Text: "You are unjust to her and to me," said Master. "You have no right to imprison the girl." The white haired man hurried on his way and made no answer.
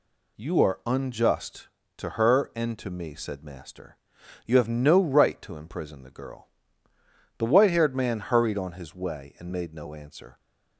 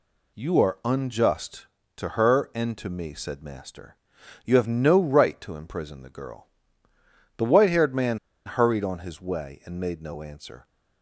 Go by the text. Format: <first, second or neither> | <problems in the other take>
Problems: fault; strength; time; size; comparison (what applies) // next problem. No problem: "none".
first | pauses between "man" and "hurried"; slight; at 8.1 s; 0.28 s long